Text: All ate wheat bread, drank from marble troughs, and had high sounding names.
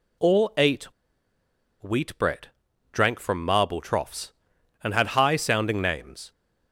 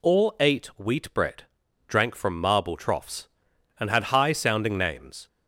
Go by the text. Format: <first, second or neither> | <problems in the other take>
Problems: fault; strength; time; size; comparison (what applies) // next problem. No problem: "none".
second | pauses between "ate" and "wheat"; at 0.8 s; 0.98 s long